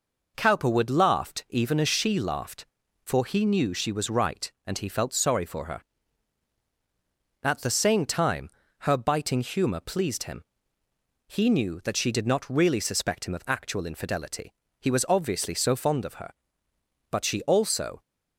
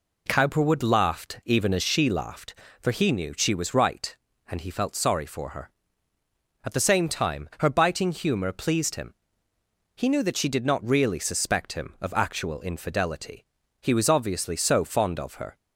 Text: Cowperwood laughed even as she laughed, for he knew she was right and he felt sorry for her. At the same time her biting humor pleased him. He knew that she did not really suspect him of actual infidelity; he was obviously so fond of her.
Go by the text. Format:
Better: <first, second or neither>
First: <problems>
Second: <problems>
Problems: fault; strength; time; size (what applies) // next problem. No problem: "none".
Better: second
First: pauses between "time" and "her"; slight; at 8.4 s; 0.30 s long // goes on to say "But she also"; noticeable; from 17.1 s on; 0.90 s long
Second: none